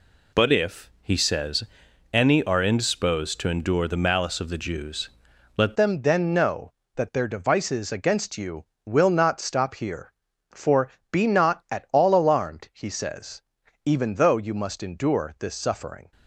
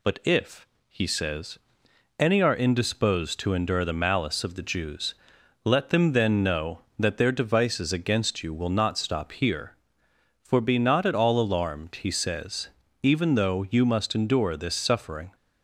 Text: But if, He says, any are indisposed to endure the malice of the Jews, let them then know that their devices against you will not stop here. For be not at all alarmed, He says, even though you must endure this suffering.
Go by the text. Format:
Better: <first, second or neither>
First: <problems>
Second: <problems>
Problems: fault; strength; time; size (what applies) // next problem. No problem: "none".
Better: second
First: changes voice at "them"; from 5.7 s on; 10.4 s long // pauses between "For" and "be"; slight; at 10.8 s; 0.22 s long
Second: none